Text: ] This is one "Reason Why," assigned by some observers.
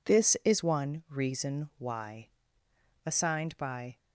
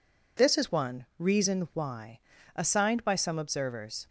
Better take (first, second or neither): second